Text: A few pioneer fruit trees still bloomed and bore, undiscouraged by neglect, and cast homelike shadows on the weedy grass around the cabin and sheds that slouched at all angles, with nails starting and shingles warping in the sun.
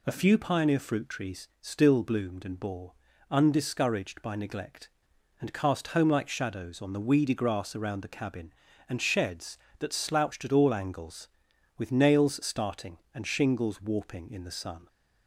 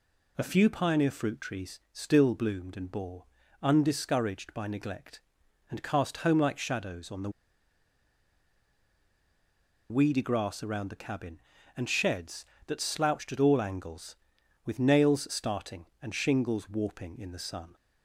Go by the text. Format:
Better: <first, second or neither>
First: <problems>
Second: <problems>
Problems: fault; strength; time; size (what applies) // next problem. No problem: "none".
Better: first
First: none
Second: pauses between "the" and "weedy"; strong; at 7.2 s; 2.6 s long